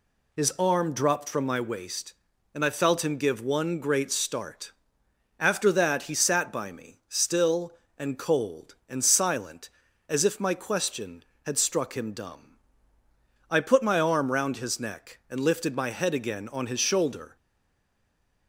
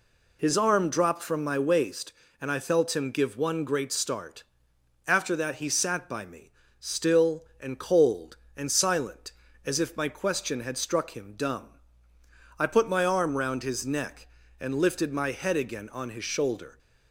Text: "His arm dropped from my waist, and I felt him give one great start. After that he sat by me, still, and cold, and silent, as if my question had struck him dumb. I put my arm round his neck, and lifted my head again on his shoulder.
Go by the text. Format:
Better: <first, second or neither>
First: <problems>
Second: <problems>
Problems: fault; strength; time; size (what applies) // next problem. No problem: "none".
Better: second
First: stays silent after the last word; from 17.3 s on; 1.1 s long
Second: none